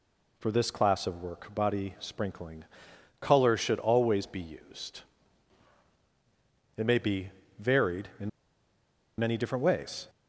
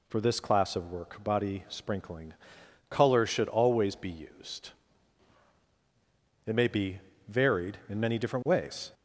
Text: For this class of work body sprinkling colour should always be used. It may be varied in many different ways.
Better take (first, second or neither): second